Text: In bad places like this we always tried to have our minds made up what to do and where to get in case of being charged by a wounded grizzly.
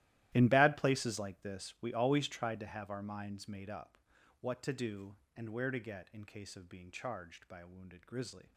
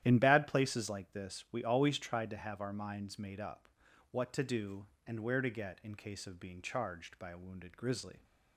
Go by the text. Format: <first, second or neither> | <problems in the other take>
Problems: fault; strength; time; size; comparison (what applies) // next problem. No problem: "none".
second | gets quieter; strong; throughout; 18 dB // starts louder than the rest; strong; until 1.3 s; 15 dB; strong in the second // pauses between "up" and "what"; at 3.9 s; 0.44 s long; also in the second